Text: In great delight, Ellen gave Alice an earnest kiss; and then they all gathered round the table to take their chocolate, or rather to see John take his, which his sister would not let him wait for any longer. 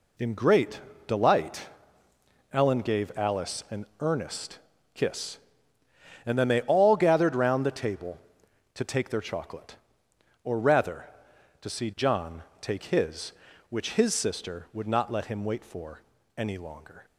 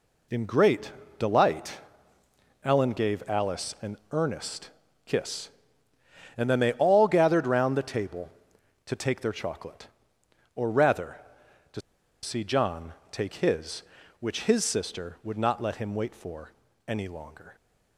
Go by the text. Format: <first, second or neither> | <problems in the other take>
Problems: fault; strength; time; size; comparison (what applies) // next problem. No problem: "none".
first | pauses between "great" and "delight"; slight; at 0.9 s; 0.26 s long; slight in the first // pauses between "earnest" and "kiss"; slight; at 4.6 s; 0.36 s long; slight in the first // pauses between "to" and "see"; at 11.8 s; 0.42 s long // pauses between "John" and "take"; slight; at 12.9 s; 0.18 s long; slight in the first // pauses between "for" and "any"; slight; at 16.5 s; 0.36 s long; slight in the first